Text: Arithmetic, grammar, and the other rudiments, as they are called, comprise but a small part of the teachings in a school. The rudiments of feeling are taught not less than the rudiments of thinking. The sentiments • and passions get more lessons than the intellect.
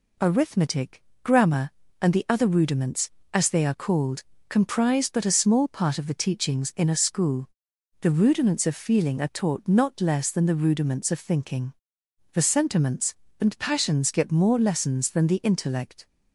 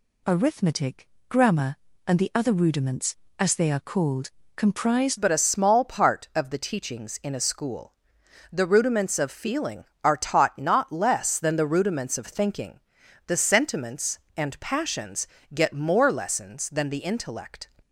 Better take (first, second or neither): first